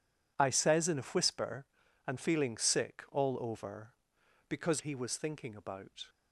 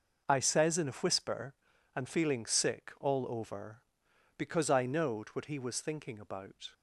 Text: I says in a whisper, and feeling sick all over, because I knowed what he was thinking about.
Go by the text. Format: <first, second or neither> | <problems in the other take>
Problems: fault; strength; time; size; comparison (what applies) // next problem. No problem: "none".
second | skips "I knowed what"; at 4.8 s